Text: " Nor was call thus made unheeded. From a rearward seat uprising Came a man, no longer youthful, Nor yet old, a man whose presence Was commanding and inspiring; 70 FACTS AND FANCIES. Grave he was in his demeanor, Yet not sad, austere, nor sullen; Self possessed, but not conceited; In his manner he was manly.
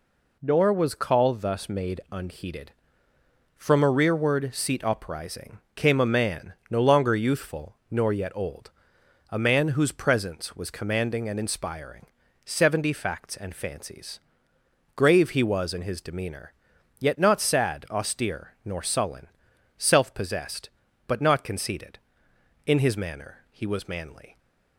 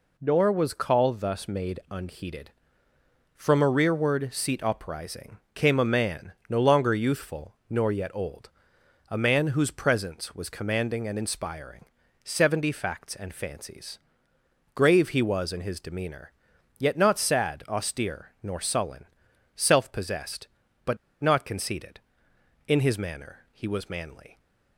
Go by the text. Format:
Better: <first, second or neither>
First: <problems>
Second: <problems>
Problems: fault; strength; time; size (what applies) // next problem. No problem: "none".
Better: first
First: pauses between "uprising" and "Came"; slight; at 5.5 s; 0.16 s long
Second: pauses between "uprising" and "Came"; slight; at 5.3 s; 0.16 s long // pauses between "but" and "not"; slight; at 20.9 s; 0.24 s long